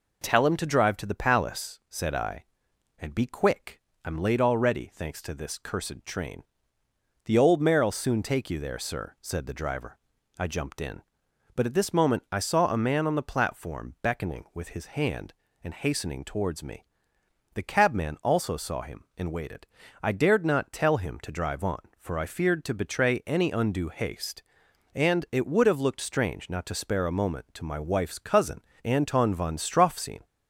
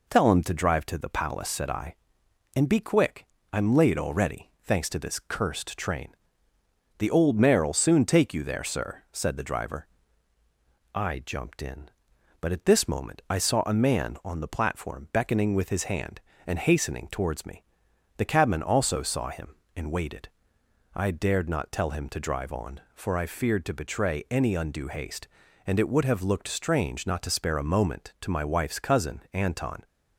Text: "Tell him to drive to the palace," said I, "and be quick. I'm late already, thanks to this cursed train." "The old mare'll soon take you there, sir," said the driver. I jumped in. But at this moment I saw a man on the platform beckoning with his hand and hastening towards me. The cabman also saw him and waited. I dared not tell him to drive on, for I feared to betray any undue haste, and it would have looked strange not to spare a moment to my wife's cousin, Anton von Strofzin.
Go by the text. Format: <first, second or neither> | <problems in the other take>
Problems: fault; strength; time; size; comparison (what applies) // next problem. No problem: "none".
first | stops before "von Strofzin"; at 29.8 s